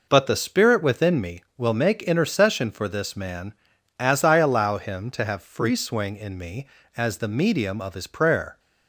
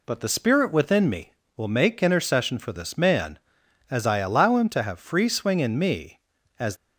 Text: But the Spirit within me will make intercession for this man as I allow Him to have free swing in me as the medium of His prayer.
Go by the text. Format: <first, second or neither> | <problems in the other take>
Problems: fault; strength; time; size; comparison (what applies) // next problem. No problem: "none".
first | stops before "the medium of His prayer"; at 6.7 s